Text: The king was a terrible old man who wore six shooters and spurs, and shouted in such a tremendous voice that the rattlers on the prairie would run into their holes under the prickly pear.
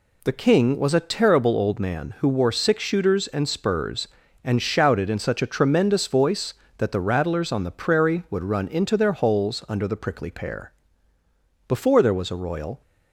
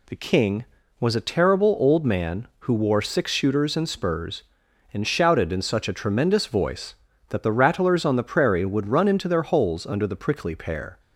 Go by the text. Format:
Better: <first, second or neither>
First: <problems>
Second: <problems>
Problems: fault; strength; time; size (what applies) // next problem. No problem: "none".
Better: second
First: goes on to say "Before there was a royal"; noticeable; from 11.6 s on; 1.1 s long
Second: none